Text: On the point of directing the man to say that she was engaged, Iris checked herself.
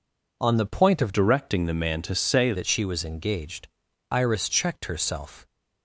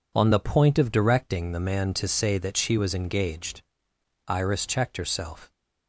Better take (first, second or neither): second